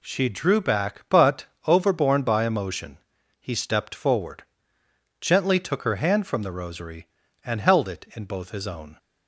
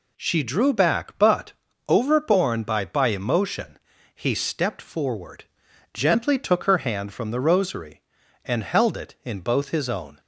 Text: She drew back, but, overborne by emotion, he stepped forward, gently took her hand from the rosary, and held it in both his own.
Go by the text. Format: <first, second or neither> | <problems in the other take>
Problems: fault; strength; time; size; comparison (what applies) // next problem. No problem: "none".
first | says "by" twice; at 2.8 s